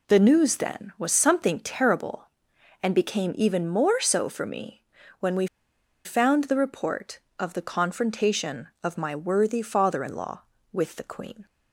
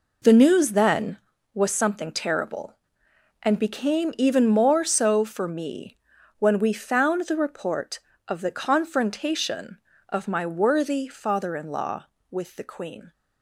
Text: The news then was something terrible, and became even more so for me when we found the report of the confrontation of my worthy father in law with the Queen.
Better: second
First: pauses between "me" and "when"; slight; at 4.8 s; 0.36 s long // pauses between "we" and "found"; noticeable; at 5.4 s; 0.58 s long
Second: pauses between "me" and "when"; at 5.9 s; 0.42 s long

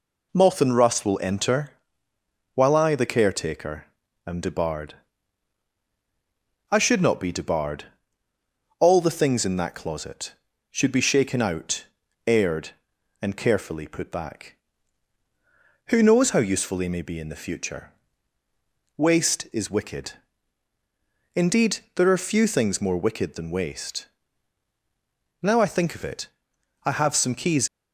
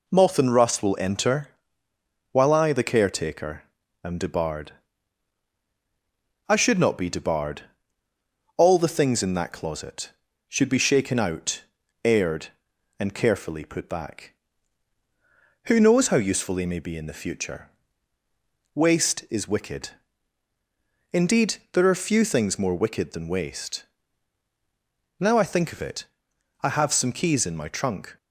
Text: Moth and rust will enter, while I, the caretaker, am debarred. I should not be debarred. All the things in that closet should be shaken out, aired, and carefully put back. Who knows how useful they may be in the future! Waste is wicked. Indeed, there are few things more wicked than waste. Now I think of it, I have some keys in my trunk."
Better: second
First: stops before "in my trunk"; at 27.6 s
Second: none

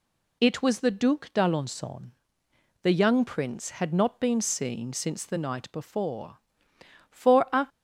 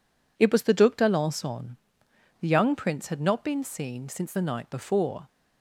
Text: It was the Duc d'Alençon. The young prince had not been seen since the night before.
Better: second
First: goes on to say "For a"; from 7.0 s on; 0.58 s long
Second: none

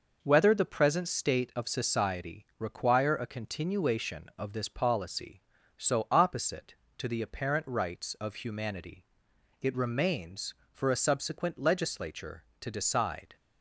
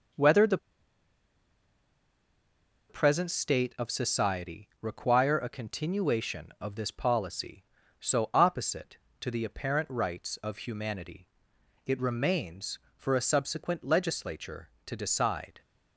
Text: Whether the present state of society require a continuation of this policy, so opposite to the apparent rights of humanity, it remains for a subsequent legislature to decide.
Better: first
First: none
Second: pauses between "the" and "present"; strong; at 0.5 s; 2.3 s long

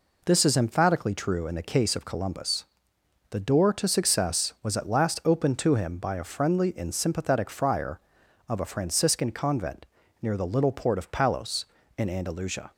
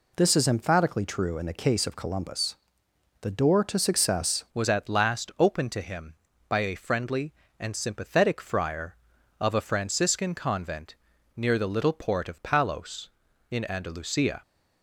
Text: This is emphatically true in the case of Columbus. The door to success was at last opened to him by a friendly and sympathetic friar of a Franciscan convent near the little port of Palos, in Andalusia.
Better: first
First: pauses between "convent" and "near"; at 9.8 s; 0.36 s long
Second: changes voice at "was"; from 4.5 s on; 9.9 s long // pauses between "convent" and "near"; at 10.9 s; 0.40 s long

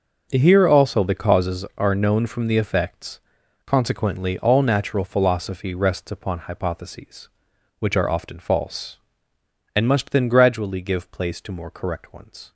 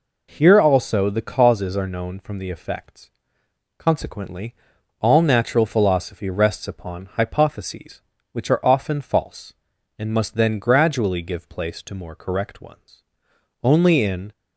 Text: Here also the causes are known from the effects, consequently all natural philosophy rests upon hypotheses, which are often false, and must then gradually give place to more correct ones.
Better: first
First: none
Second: pauses between "consequently" and "all"; noticeable; at 4.5 s; 0.48 s long // goes on to say "Only in"; noticeable; from 13.6 s on; 0.68 s long

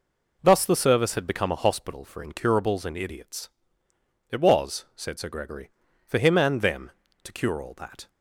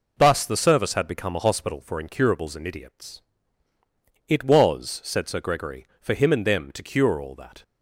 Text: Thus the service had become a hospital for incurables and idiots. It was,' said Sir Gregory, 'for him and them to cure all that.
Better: neither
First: none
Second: none

